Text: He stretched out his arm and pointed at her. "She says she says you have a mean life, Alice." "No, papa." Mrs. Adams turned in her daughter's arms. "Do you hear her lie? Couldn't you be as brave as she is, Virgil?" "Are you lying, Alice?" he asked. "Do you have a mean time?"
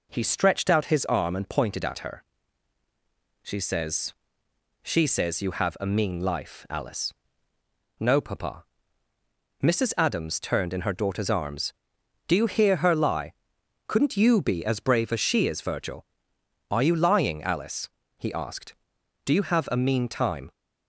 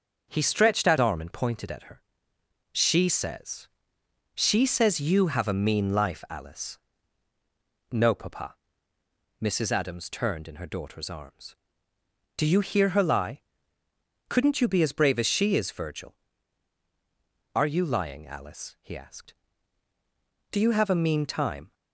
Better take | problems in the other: first | starts louder than the rest; until 1.3 s; 6.5 dB // skips "his"; at 0.9 s // pauses between "says" and "she"; noticeable; at 3.6 s; 0.68 s long; noticeable in the first

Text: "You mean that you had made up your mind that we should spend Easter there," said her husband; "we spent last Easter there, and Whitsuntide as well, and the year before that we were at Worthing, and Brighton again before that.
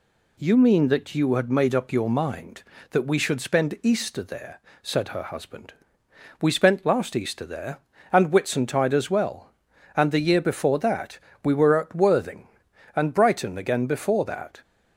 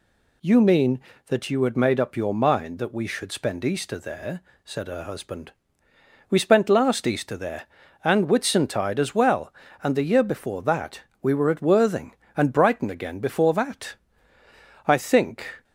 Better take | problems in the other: first | pauses between "that" and "we"; slight; at 11.0 s; 0.18 s long; slight in the first // goes on to say "I think"; noticeable; from 14.8 s on; 0.78 s long

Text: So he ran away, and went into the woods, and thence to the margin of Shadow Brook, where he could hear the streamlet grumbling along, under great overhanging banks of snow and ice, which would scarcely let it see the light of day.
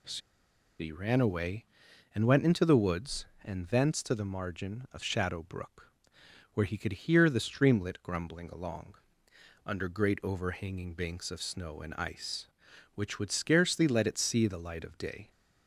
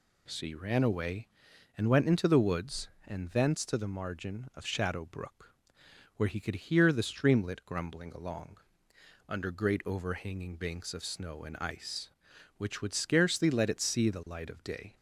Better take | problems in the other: second | pauses between "So" and "he"; noticeable; at 0.2 s; 0.61 s long

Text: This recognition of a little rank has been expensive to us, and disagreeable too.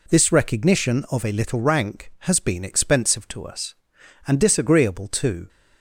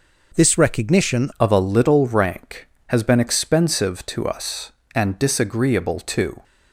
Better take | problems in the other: first | changes voice at "of"; from 1.3 s on; 5.1 s long

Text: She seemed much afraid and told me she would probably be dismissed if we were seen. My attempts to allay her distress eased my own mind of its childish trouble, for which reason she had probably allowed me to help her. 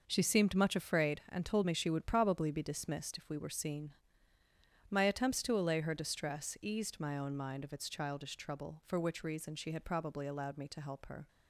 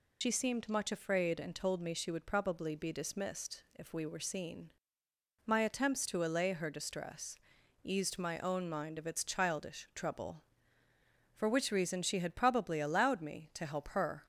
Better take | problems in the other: first | loses the start of "She"; at 0.2 s; 85 ms // pauses between "distress" and "eased"; at 7.3 s; 0.44 s long

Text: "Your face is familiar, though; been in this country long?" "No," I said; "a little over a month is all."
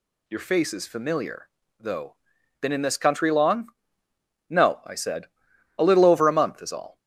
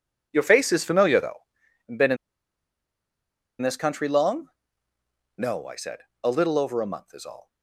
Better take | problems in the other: first | pauses between "in" and "this"; strong; at 2.1 s; 1.4 s long

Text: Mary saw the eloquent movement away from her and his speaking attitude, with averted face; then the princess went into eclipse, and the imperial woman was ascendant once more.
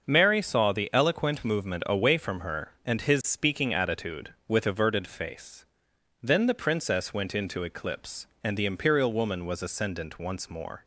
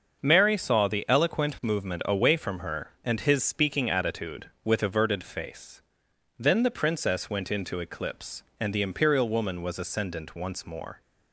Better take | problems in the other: neither | starts louder than the rest; the same in both

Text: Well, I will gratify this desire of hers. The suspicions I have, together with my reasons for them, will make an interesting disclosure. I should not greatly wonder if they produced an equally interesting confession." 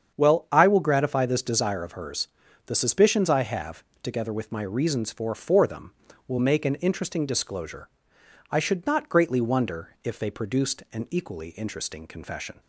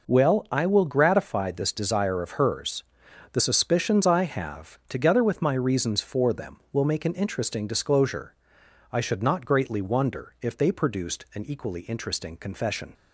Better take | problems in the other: second | starts louder than the rest; strong; until 1.1 s; 7.5 dB // says "for" twice; at 5.3 s

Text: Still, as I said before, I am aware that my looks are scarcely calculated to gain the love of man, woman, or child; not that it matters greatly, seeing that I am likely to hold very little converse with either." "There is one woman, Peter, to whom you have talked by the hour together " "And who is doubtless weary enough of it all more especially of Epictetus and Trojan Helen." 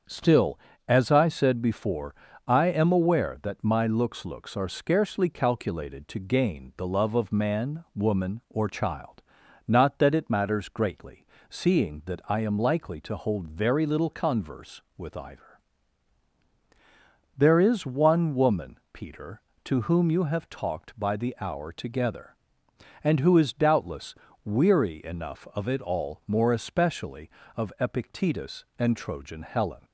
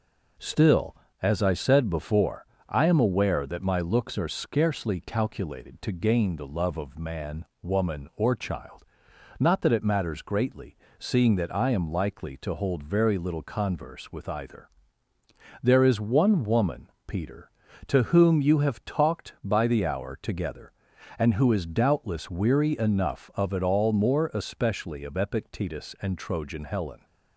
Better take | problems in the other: second | starts louder than the rest; until 1.3 s; 7 dB // says "looks" twice; at 4.2 s // pauses between "doubtless" and "weary"; slight; at 24.1 s; 0.30 s long

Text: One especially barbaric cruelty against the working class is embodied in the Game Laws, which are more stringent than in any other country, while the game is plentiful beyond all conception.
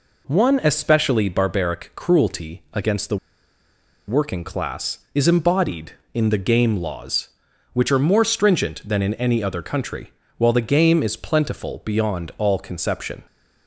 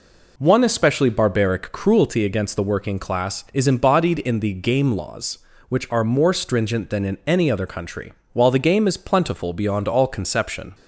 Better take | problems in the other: second | pauses between "the" and "working"; noticeable; at 3.1 s; 0.91 s long

